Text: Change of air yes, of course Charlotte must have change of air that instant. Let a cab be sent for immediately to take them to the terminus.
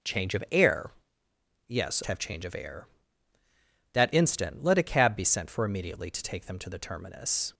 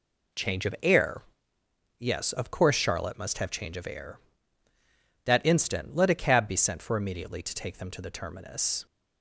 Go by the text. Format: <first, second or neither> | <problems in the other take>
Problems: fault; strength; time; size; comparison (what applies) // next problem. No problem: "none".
second | starts louder than the rest; strong; until 1.8 s; 7.5 dB // pauses between "air" and "yes"; noticeable; at 0.9 s; 0.76 s long; noticeable in the second // skips "of course Charlotte must"; at 2.0 s